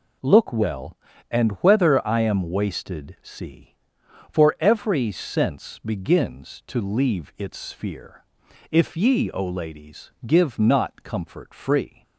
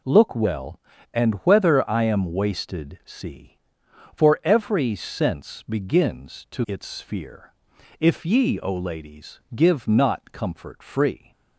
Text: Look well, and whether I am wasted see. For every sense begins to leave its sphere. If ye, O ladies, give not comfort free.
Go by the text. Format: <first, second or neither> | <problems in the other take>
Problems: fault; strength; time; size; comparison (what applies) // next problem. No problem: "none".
first | skips "leave"; at 6.6 s